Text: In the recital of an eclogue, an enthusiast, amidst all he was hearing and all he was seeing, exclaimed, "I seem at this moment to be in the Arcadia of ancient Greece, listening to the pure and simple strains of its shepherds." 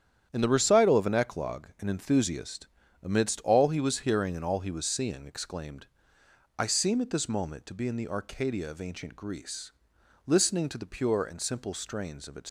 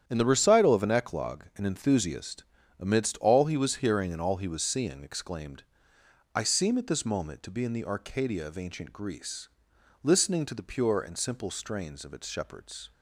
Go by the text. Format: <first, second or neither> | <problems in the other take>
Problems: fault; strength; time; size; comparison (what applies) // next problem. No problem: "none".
second | starts louder than the rest; strong; until 1.3 s; 9.5 dB; strong in the second // stops before "shepherds"; at 12.4 s